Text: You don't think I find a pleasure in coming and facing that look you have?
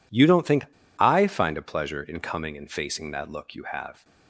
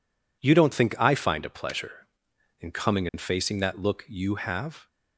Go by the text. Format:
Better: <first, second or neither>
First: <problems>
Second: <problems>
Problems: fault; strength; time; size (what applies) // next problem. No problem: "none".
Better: second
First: pauses between "think" and "I"; slight; at 0.6 s; 0.33 s long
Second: none